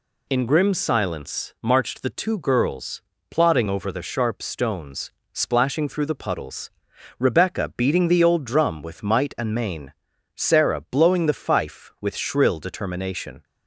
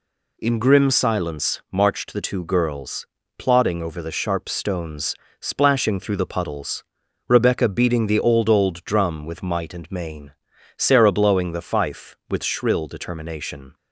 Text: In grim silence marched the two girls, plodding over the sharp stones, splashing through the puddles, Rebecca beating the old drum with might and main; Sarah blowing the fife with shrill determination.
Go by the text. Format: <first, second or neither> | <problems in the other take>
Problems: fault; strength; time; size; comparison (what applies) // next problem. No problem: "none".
first | says "old" twice; at 8.4 s